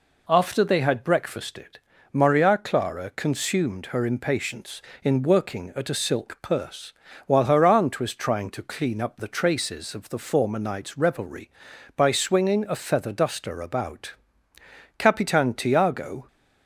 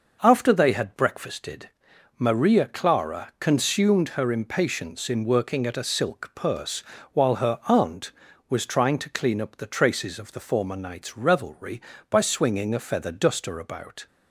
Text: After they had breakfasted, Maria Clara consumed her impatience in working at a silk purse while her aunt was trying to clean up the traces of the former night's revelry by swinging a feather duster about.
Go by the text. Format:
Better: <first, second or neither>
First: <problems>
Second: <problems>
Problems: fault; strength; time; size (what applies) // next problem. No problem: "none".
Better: second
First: pauses between "purse" and "while"; slight; at 6.9 s; 0.34 s long // goes on to say "Capitan Tiago"; noticeable; from 14.9 s on; 1.3 s long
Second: pauses between "purse" and "while"; slight; at 6.8 s; 0.28 s long